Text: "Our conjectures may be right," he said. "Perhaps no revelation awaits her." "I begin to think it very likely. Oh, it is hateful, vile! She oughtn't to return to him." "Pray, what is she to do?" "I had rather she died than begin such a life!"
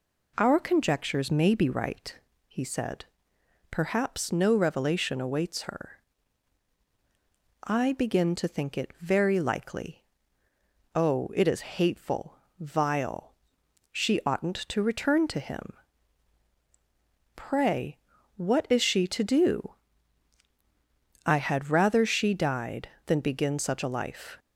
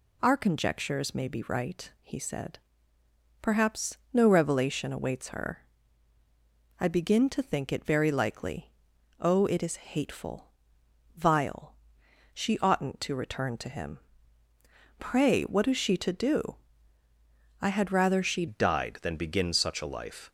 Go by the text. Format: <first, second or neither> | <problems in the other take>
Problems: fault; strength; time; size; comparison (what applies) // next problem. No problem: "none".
first | changes voice at "died"; from 18.4 s on; 1.9 s long